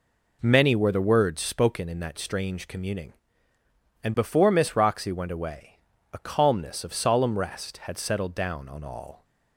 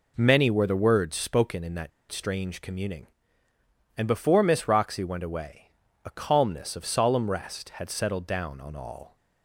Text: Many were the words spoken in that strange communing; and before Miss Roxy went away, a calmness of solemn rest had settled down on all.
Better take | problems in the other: first | pauses between "that" and "strange"; slight; at 1.9 s; 0.21 s long

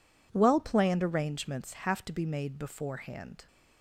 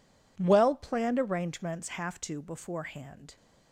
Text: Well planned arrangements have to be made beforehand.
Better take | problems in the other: first | skips "be made"; at 2.4 s

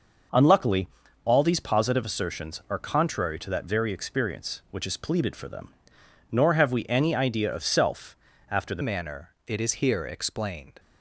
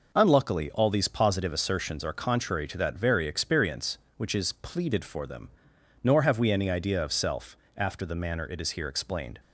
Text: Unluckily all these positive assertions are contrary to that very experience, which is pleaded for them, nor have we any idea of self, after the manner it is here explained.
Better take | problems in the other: second | pauses between "Unluckily" and "all"; slight; at 0.8 s; 0.36 s long // changes voice at "manner"; from 8.8 s on; 1.9 s long

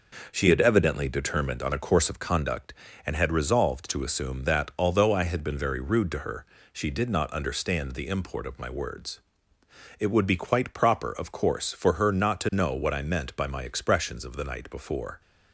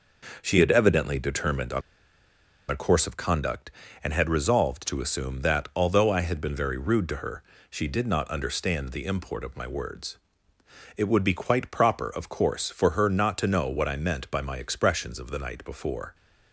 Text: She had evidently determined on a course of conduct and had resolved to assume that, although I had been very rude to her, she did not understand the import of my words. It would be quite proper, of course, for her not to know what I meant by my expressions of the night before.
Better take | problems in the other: first | pauses between "on" and "a"; noticeable; at 1.8 s; 0.89 s long

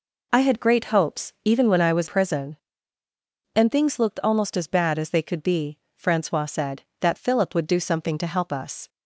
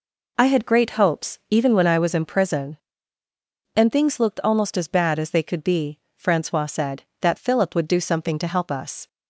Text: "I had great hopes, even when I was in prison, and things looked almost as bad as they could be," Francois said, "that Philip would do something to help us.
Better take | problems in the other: second | skips "in"; at 2.0 s

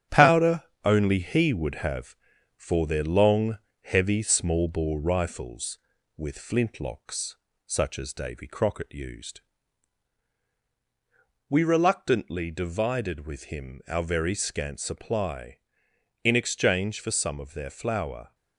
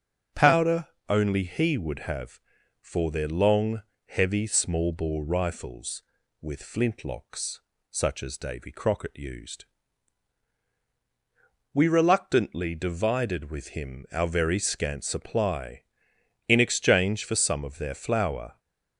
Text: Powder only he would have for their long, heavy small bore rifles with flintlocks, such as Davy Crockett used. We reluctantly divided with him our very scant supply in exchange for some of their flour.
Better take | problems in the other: second | gets quieter; noticeable; throughout; 5.5 dB // starts louder than the rest; strong; until 1.3 s; 10 dB; strong in the second // pauses between "Powder" and "only"; slight; at 0.6 s; 0.22 s long; slight in the second

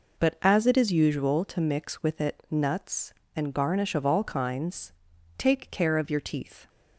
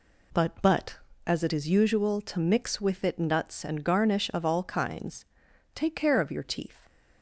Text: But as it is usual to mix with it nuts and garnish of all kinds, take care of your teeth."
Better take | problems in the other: first | says "But" twice; at 0.6 s

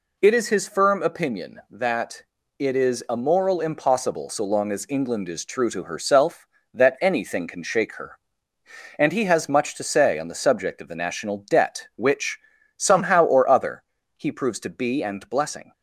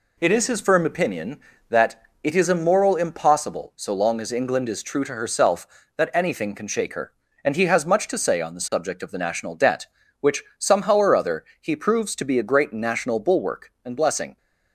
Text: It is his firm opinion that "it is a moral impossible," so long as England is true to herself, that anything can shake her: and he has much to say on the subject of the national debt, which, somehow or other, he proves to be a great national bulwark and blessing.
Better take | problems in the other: second | pauses between "that" and "it"; slight; at 2.2 s; 0.36 s long; slight in the second // skips "a great national bulwark"; at 15.0 s

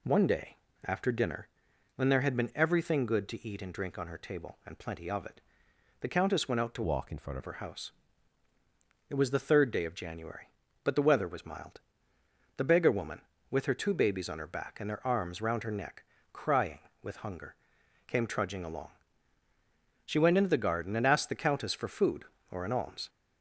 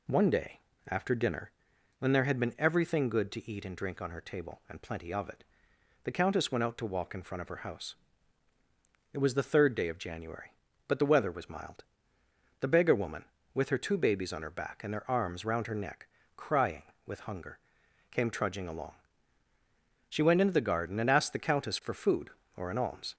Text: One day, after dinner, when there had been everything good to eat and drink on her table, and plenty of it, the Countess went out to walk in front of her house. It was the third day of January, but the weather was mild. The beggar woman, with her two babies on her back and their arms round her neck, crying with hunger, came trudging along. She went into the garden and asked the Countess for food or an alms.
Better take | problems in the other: second | changes voice from "walk" to "front"; from 6.8 to 7.3 s; 0.5 s long

